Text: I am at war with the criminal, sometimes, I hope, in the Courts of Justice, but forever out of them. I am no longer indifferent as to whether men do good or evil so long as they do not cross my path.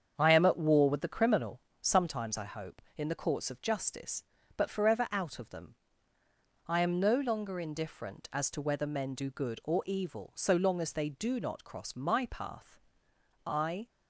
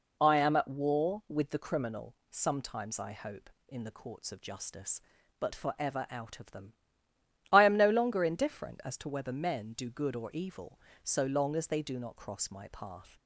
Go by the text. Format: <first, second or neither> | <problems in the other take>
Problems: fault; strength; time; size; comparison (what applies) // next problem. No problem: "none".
second | starts louder than the rest; strong; until 1.1 s; 7.5 dB // goes on to say "I"; slight; from 13.4 s on; 0.42 s long